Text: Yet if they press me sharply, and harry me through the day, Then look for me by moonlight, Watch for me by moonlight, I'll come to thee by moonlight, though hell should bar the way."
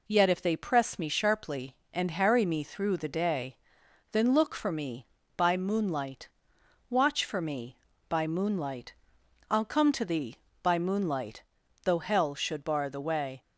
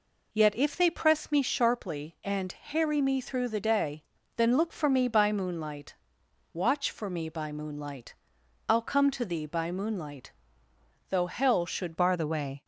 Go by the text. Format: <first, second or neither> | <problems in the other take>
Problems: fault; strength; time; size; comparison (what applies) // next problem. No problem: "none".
first | changes voice at "bar"; from 11.9 s on; 0.7 s long